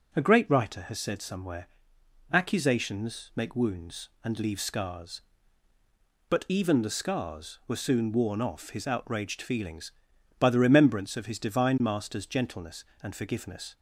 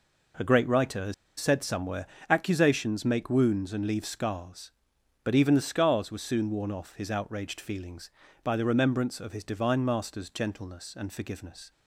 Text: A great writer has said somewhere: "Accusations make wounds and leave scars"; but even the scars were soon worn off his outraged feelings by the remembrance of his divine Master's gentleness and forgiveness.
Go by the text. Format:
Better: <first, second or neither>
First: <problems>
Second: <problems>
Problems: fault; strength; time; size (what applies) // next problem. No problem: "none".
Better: first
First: none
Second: pauses between "has" and "said"; slight; at 1.1 s; 0.25 s long